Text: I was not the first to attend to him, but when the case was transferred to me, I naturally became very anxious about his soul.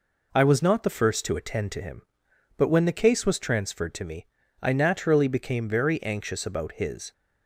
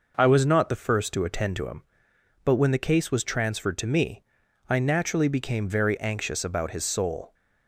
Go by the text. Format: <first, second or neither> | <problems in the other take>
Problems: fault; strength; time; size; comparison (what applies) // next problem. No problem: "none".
second | stops before "soul"; at 7.1 s